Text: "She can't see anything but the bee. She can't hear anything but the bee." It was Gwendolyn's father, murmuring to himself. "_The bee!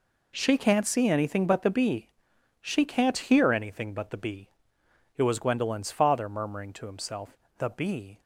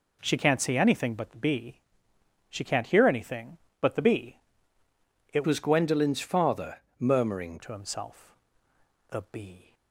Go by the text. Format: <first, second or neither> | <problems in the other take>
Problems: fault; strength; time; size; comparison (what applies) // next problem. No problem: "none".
first | changes voice from "was" to "murmuring"; from 5.4 to 7.5 s; 2.1 s long